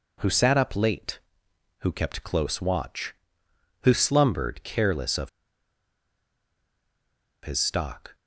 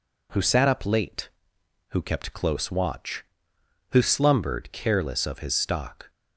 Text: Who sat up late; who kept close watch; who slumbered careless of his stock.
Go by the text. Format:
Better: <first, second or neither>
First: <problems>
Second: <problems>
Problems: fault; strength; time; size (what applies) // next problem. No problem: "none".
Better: second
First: pauses between "of" and "his"; strong; at 5.2 s; 2.1 s long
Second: none